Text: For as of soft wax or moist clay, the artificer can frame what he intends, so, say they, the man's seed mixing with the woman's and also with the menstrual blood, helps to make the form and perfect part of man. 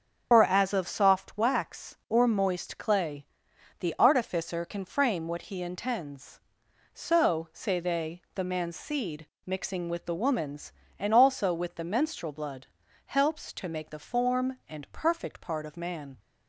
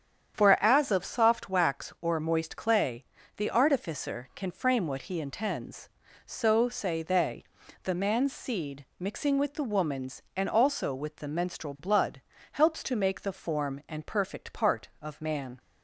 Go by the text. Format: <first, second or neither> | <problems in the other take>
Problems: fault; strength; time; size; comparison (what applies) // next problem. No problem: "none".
second | loses the start of "For"; at 0.3 s; 75 ms // starts louder than the rest; until 1.3 s; 7 dB; strong in the second // pauses between "seed" and "mixing"; slight; at 9.2 s; 0.18 s long; slight in the second